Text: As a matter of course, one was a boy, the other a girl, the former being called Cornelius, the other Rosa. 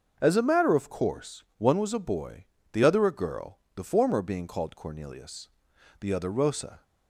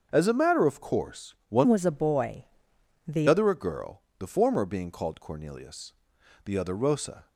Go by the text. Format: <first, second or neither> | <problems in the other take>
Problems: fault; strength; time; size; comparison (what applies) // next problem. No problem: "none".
first | starts louder than the rest; until 1.1 s; 6.5 dB; also in the first // changes voice from "was" to "the"; from 1.6 to 3.2 s; 1.6 s long